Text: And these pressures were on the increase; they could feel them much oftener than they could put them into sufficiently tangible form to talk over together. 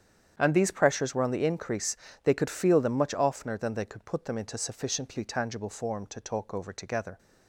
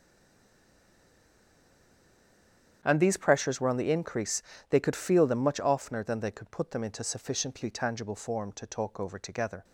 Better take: first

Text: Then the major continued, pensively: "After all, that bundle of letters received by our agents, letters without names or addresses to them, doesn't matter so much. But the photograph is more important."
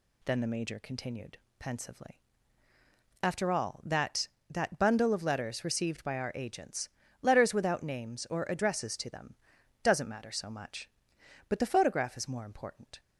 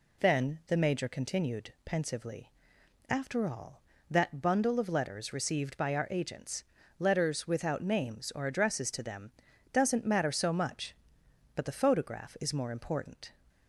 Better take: second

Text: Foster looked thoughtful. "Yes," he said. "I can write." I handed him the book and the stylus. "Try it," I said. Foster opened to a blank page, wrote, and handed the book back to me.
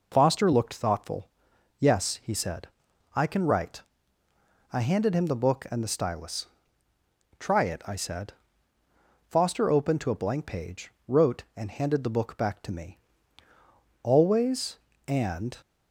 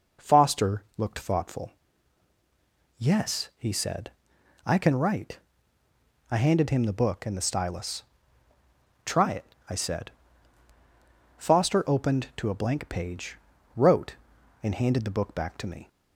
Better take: second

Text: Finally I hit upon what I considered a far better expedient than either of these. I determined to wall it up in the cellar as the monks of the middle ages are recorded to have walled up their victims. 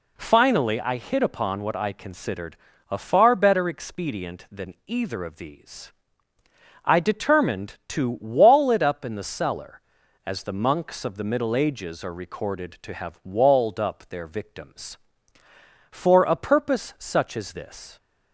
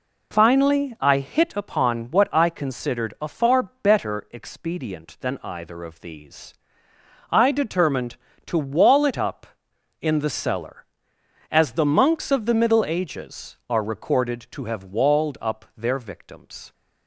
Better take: second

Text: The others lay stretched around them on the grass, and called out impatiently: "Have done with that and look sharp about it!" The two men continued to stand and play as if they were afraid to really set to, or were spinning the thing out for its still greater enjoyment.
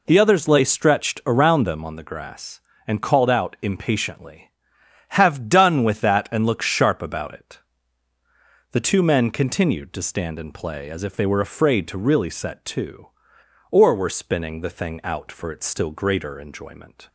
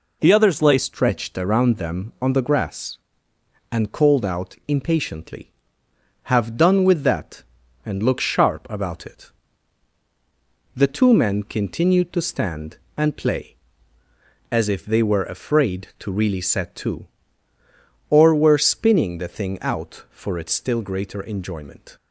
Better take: first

